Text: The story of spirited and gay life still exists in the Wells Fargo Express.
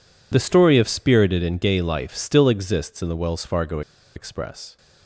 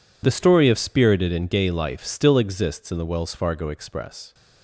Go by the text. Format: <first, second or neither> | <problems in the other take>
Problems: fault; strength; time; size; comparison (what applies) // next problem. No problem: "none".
second | pauses between "Fargo" and "Express"; slight; at 3.8 s; 0.35 s long